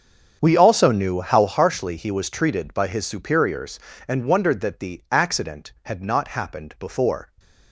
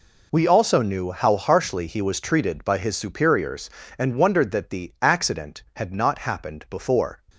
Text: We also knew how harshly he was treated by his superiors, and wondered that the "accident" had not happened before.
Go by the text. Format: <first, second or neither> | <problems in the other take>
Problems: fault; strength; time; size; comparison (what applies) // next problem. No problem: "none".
second | starts louder than the rest; strong; until 1.6 s; 7.5 dB